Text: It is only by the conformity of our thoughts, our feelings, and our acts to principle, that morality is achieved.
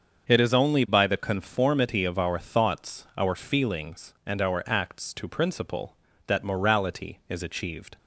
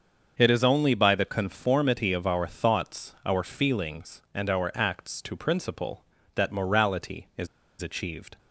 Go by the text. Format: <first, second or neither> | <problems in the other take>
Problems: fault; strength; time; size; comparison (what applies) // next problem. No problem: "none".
first | starts louder than the rest; until 1.3 s; 6.5 dB; also in the first // pauses between "is" and "achieved"; slight; at 7.4 s; 0.34 s long